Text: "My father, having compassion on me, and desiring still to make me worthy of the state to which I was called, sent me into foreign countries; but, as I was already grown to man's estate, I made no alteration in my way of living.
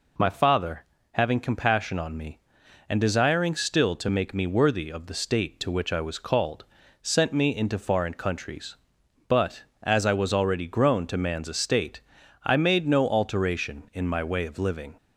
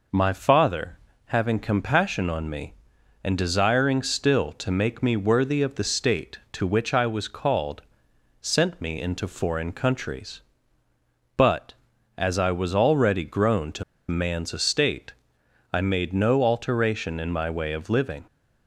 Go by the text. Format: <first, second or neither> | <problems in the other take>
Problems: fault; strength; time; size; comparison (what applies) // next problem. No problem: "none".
first | pauses between "to" and "man's"; slight; at 13.8 s; 0.25 s long